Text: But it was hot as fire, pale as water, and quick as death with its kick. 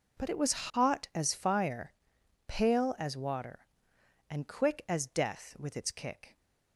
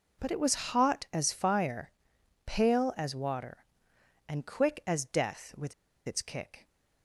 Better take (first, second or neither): first